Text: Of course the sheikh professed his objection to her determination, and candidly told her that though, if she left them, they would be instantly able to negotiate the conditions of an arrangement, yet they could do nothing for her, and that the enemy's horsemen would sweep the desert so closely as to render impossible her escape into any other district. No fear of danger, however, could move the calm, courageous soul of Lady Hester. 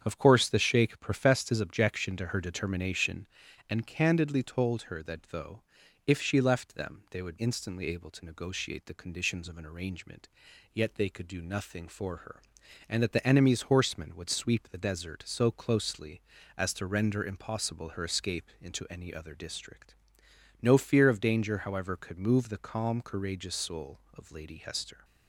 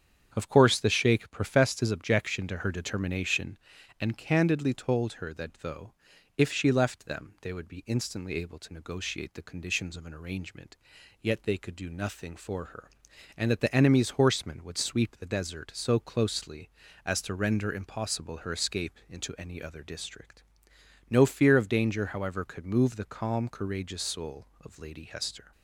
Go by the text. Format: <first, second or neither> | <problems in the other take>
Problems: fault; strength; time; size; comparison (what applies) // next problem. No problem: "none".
second | starts louder than the rest; strong; until 1.0 s; 8 dB; strong in the second // skips "be"; at 7.3 s